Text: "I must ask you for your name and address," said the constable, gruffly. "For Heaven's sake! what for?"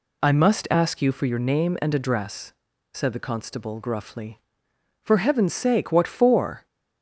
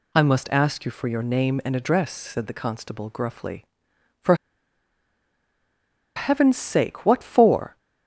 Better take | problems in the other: first | pauses between "For" and "Heaven's"; strong; at 4.3 s; 1.7 s long

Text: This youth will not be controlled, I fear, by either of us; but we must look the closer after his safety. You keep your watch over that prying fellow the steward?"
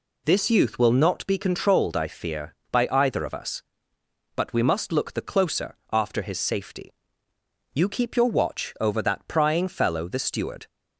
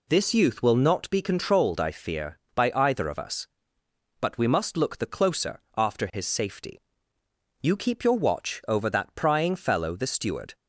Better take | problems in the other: neither | pauses between "closer" and "after"; slight; the same in both

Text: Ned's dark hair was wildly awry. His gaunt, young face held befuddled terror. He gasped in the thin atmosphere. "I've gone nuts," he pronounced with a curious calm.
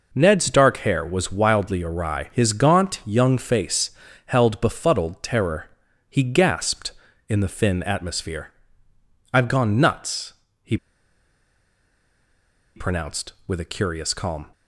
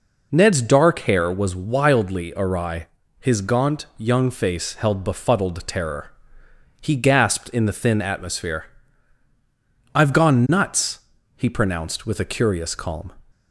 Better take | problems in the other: second | pauses between "face" and "held"; slight; at 3.9 s; 0.36 s long // pauses between "he" and "pronounced"; strong; at 10.7 s; 1.9 s long

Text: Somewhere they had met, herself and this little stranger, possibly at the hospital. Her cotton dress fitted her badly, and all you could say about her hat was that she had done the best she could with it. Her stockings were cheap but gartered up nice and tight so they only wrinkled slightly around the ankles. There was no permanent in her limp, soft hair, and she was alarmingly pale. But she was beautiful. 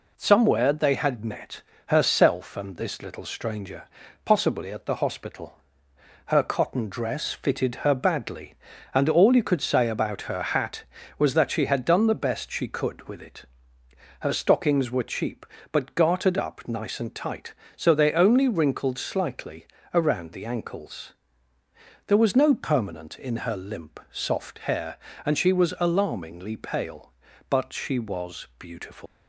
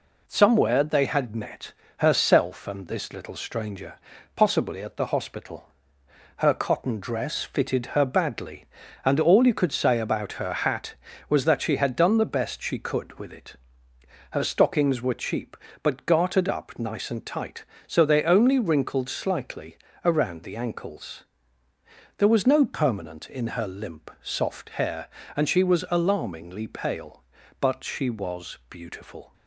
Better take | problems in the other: second | pauses between "slightly" and "around"; slight; at 19.6 s; 0.26 s long; slight in the second // leaves "beautiful" unfinished; at 29.0 s; 160 ms

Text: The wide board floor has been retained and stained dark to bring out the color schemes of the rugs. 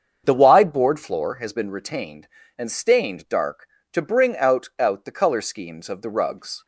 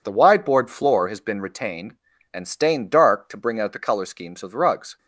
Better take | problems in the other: second | starts louder than the rest; until 1.2 s; 7 dB // says "out" twice; at 4.7 s

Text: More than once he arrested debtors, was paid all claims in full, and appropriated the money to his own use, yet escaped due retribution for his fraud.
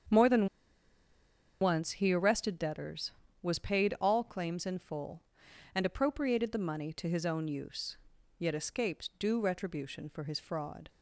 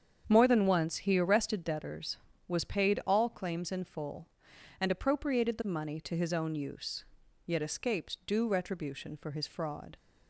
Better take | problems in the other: second | starts louder than the rest; strong; until 2.2 s; 7.5 dB; strong in the second // pauses between "than" and "once"; at 0.4 s; 1.1 s long

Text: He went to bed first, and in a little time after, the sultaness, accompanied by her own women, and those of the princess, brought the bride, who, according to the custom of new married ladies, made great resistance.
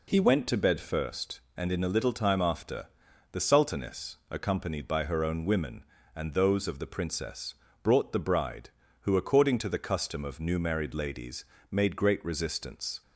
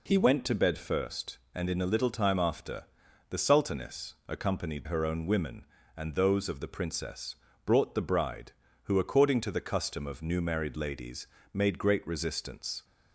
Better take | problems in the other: first | skips "by"; at 4.8 s

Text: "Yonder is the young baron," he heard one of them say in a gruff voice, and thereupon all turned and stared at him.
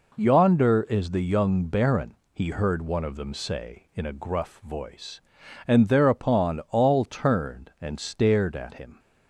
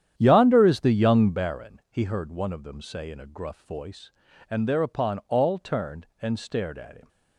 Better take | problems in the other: first | starts louder than the rest; strong; until 1.4 s; 10 dB

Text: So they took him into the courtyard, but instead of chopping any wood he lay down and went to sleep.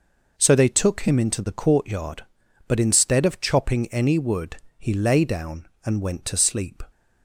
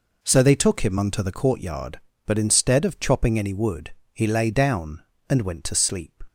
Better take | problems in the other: first | says "unto" for "into"; at 0.9 s // pauses between "wood" and "he"; slight; at 3.9 s; 0.20 s long; slight in the first

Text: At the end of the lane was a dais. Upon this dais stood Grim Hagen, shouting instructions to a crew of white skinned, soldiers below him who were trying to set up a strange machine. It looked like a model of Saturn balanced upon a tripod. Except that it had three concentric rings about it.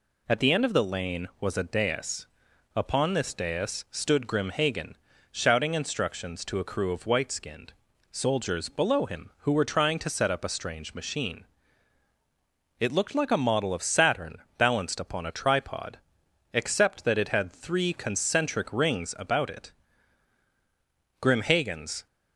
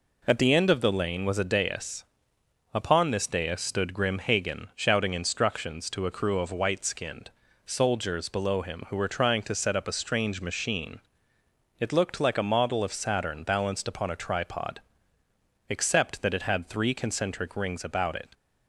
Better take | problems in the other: second | pauses between "Saturn" and "balanced"; slight; at 14.3 s; 0.20 s long // goes on to say "Grim Hagen's"; noticeable; from 21.1 s on; 0.86 s long

